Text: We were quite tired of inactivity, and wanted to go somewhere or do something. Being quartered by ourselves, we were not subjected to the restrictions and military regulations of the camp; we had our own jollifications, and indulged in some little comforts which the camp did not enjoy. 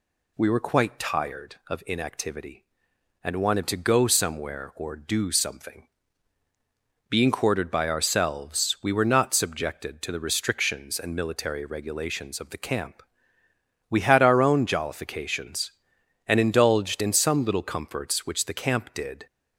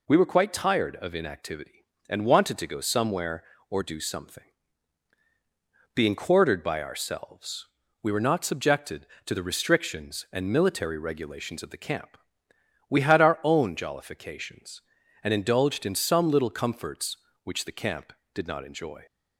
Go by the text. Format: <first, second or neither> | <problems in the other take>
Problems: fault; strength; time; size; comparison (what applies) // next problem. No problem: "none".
second | stops before "not enjoy"; at 19.2 s